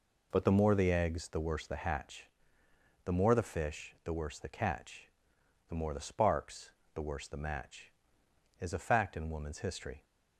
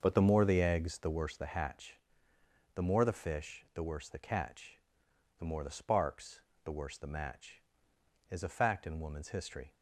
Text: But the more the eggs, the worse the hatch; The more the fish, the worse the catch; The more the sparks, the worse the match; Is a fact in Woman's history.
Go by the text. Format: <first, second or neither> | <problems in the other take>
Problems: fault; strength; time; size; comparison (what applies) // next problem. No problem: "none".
first | starts louder than the rest; until 1.3 s; 6.5 dB